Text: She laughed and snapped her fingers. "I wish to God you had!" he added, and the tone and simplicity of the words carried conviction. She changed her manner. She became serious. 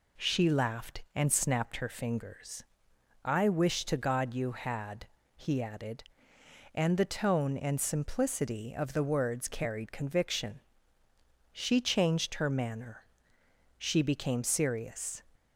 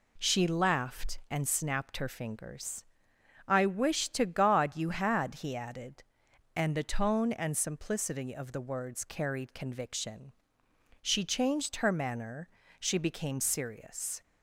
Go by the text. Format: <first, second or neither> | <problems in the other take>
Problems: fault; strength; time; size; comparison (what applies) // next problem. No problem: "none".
neither | none